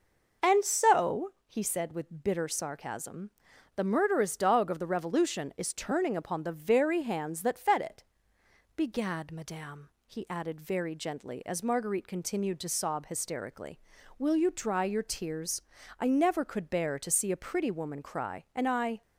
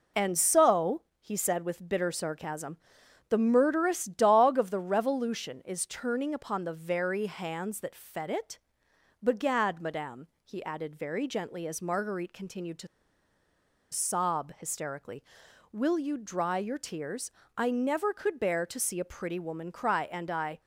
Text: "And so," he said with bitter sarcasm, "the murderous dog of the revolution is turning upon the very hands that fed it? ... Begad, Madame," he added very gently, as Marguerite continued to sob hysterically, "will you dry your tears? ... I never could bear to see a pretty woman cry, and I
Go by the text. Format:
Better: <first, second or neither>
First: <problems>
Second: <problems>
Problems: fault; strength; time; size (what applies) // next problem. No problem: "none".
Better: first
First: none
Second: pauses between "to" and "sob"; at 12.8 s; 1.0 s long